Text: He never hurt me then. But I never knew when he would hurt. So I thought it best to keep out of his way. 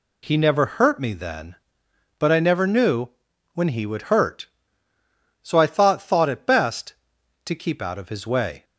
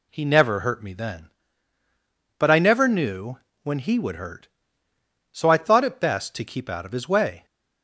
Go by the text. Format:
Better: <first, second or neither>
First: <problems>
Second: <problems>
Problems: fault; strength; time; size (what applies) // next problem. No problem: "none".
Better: second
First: pauses between "knew" and "when"; at 3.0 s; 0.42 s long // says "thought" twice; at 5.9 s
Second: pauses between "knew" and "when"; slight; at 3.3 s; 0.26 s long